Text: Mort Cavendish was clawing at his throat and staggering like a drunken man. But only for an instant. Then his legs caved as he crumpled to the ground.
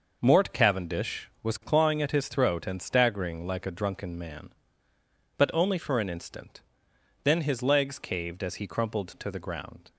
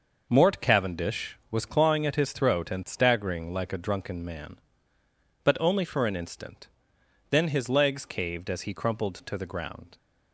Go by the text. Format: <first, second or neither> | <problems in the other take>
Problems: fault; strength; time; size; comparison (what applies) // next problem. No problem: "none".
neither | none